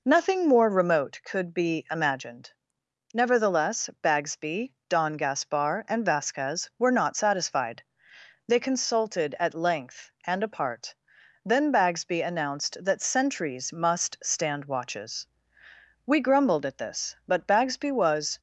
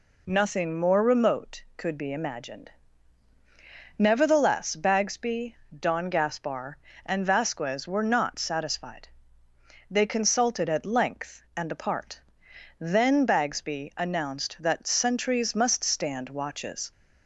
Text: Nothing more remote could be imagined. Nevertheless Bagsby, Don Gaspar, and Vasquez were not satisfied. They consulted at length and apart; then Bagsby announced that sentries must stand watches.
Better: second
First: goes on to say "We grumbled at this but Bagsby was"; strong; from 16.0 s on; 2.3 s long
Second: none

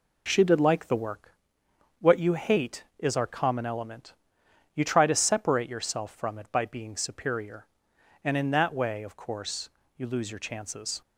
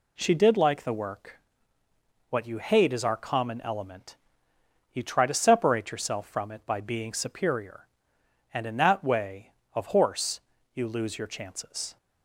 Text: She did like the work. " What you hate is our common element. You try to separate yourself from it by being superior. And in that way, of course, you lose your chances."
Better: first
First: none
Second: says "horse" for "course"; at 9.8 s

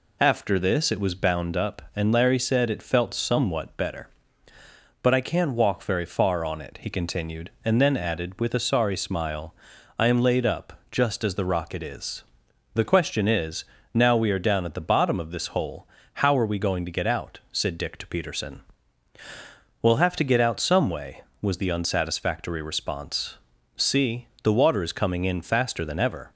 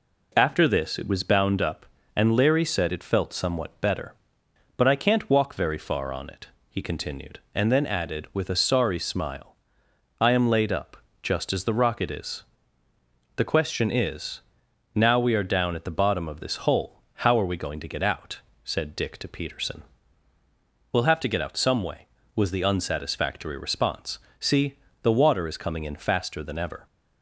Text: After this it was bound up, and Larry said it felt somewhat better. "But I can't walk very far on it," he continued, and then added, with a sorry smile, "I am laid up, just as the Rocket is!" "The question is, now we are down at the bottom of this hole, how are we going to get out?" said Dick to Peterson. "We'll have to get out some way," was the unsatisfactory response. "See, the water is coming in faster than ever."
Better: neither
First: none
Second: none

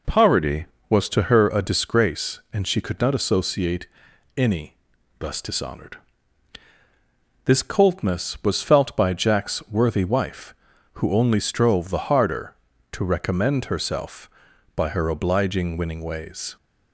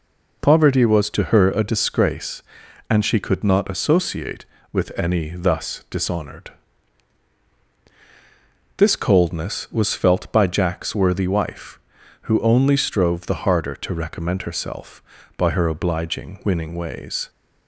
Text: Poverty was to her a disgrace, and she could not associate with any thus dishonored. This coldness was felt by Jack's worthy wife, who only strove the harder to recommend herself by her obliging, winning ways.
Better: second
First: skips "with"; at 4.1 s // pauses between "any" and "thus"; at 4.7 s; 0.42 s long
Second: none

